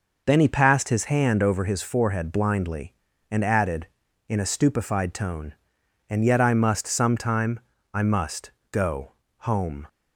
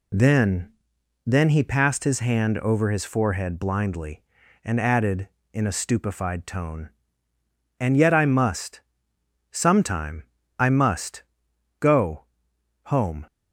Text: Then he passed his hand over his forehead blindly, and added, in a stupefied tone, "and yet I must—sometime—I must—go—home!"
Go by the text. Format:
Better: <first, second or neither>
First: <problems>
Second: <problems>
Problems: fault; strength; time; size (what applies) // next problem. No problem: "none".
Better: first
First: none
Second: says "Then" twice; at 1.2 s